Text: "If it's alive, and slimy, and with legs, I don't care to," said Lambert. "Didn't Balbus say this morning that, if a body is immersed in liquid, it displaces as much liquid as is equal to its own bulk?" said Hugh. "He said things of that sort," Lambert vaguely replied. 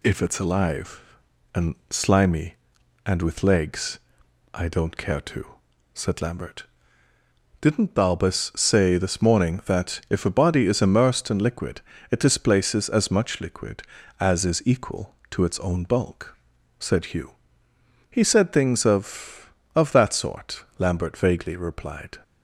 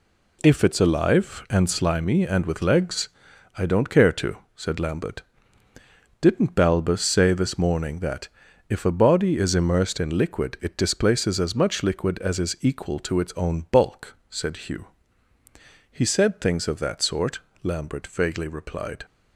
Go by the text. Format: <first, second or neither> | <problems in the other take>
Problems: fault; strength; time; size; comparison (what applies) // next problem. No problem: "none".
second | says "of" twice; at 19.7 s